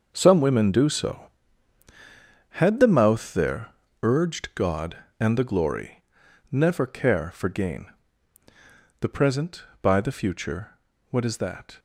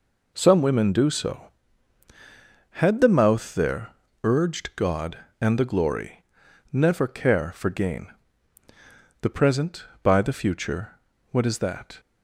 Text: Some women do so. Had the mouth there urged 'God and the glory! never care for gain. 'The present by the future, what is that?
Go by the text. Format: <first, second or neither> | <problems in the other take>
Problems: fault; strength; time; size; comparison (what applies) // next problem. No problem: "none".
second | gets quieter; strong; throughout; 11.5 dB // pauses between "there" and "urged"; slight; at 3.7 s; 0.32 s long; slight in the second